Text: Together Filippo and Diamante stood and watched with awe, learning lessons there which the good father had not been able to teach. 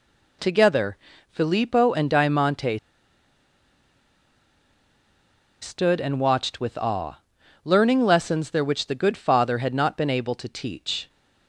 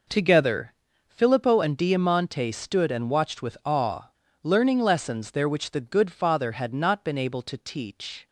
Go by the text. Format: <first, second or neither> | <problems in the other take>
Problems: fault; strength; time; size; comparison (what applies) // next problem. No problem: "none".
second | pauses between "Together" and "Filippo"; slight; at 0.9 s; 0.32 s long; slight in the second // pauses between "Diamante" and "stood"; strong; at 2.7 s; 2.8 s long